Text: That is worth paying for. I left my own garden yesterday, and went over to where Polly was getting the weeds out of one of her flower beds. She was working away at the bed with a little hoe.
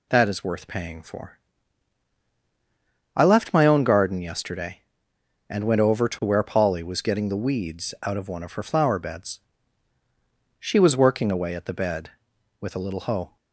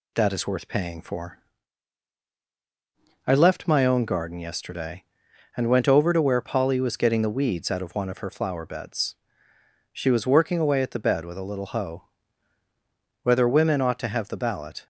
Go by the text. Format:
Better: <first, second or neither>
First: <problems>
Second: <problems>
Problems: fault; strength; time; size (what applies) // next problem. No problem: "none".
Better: first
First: none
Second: goes on to say "Whether women ought to have the ballot"; from 13.2 s on; 1.6 s long